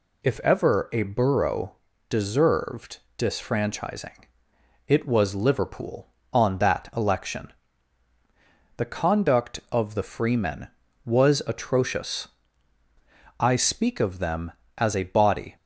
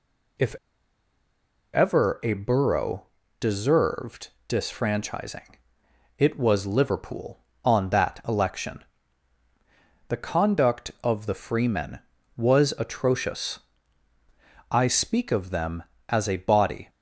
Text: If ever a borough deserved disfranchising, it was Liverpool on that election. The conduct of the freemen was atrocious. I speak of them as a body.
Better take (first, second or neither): first